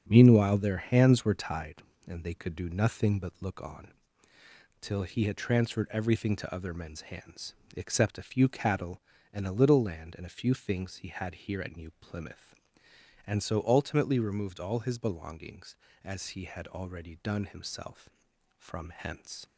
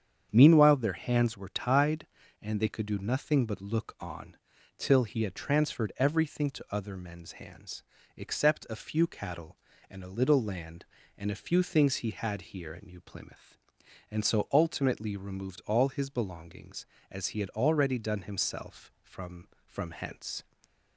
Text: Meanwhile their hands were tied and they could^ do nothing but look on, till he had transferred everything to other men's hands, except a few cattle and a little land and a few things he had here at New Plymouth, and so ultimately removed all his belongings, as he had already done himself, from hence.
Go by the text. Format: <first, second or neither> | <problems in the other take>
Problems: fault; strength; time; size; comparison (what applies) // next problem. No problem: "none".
first | starts louder than the rest; strong; until 1.3 s; 8 dB; strong in the first // says "from" twice; at 19.6 s // stays silent after the last word; slight; from 20.4 s on; 0.5 s long